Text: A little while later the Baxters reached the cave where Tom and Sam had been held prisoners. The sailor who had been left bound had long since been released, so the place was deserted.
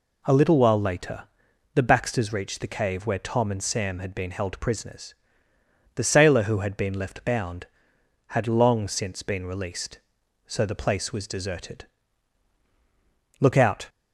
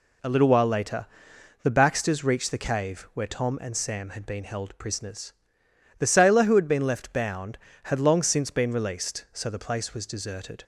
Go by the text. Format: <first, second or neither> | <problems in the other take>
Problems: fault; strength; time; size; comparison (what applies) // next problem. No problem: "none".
second | pauses between "later" and "the"; noticeable; at 1.2 s; 0.50 s long; noticeable in the second // goes on to say "Look out"; slight; from 13.4 s on; 0.48 s long